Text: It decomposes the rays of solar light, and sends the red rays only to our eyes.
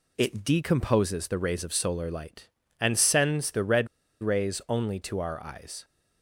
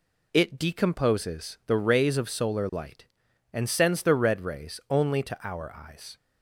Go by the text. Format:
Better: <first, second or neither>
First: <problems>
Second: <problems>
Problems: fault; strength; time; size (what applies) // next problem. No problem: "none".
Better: second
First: pauses between "red" and "rays"; slight; at 3.8 s; 0.35 s long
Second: none